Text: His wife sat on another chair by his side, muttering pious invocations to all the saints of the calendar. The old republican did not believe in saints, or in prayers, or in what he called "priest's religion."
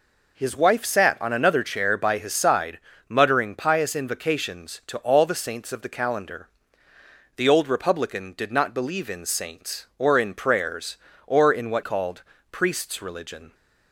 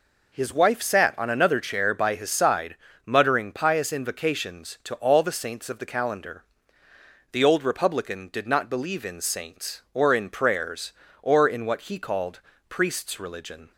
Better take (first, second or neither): second